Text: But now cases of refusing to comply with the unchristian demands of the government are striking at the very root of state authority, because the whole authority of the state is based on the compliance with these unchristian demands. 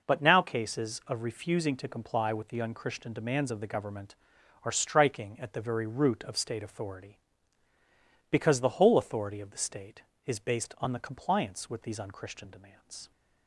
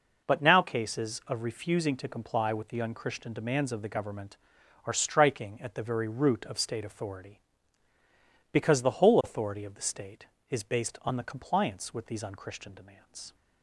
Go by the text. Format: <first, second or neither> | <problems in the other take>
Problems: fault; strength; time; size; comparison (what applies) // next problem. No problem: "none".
neither | none